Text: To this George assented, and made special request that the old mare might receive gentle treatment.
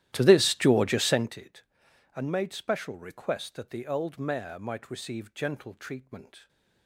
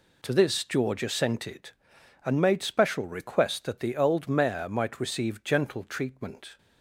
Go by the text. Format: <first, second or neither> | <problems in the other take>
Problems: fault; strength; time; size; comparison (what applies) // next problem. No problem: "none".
second | starts louder than the rest; strong; until 1.4 s; 13.5 dB